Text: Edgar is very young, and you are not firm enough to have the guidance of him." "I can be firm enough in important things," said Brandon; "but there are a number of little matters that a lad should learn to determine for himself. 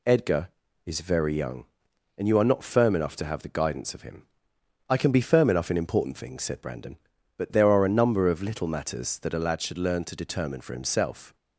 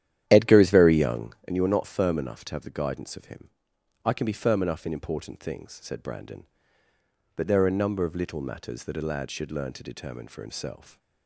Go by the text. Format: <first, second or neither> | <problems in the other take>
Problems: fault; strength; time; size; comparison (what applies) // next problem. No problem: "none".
first | starts louder than the rest; strong; until 1.6 s; 11 dB